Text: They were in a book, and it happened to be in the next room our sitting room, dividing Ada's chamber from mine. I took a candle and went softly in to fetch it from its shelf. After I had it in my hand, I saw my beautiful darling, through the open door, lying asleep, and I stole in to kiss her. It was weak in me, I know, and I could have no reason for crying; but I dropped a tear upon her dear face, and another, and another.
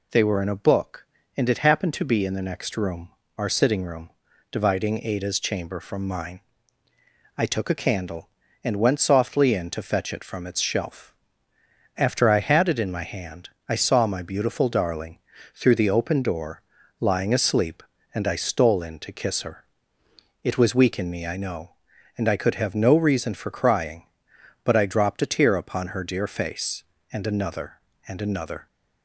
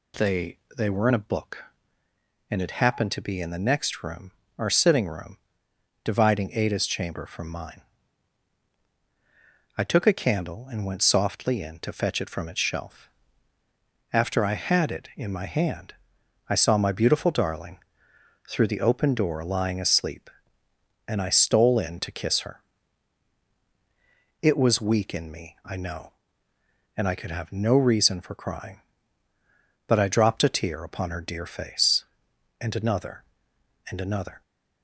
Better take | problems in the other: first | says "They" twice; at 0.7 s // pauses between "room" and "our"; slight; at 4.2 s; 0.28 s long; slight in the first

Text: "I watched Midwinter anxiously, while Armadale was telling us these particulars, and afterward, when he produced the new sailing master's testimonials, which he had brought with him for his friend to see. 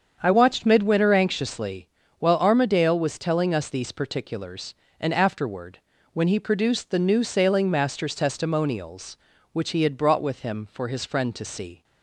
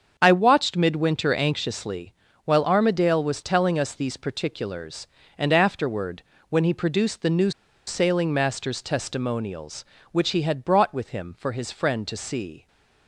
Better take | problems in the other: first | starts louder than the rest; until 1.1 s; 7 dB; strong in the first // pauses between "new" and "sailing"; slight; at 7.5 s; 0.36 s long

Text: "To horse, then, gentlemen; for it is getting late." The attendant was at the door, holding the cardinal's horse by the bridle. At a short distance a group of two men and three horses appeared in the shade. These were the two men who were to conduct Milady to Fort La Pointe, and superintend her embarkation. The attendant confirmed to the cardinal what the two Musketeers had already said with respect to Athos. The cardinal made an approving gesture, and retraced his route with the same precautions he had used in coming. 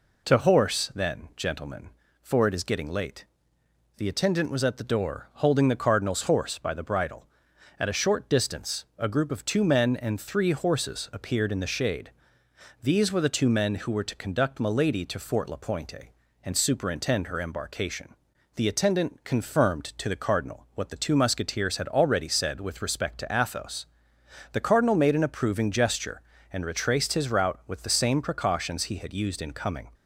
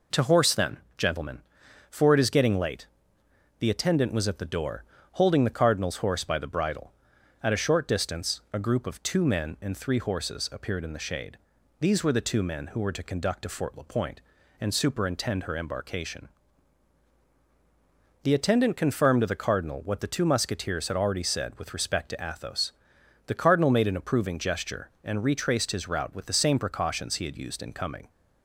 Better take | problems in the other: first | skips "Milady"; at 13.4 s

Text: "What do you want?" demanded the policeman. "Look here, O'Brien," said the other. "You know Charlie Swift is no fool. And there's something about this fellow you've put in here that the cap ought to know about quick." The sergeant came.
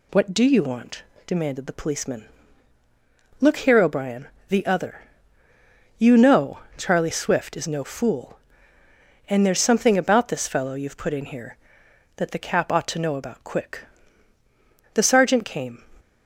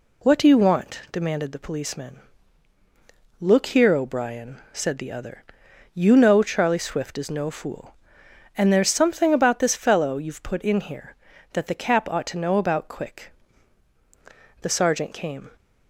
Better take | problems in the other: second | skips "said"; at 4.3 s // pauses between "know" and "Charlie"; slight; at 6.5 s; 0.18 s long

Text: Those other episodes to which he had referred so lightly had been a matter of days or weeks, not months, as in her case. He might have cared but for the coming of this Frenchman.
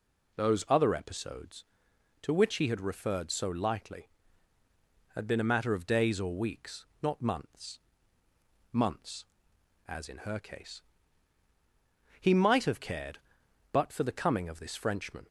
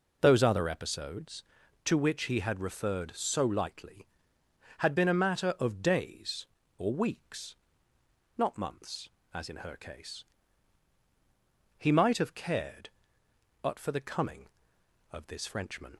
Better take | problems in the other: second | says "months" twice; at 8.7 s

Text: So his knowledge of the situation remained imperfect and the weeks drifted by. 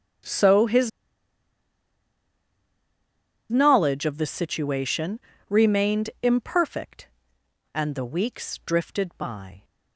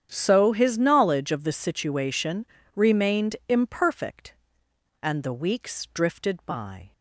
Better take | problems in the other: second | starts louder than the rest; strong; until 3.8 s; 9 dB; strong in the second // pauses between "his" and "knowledge"; strong; at 0.8 s; 2.6 s long // pauses between "situation" and "remained"; slight; at 5.1 s; 0.30 s long; slight in the second

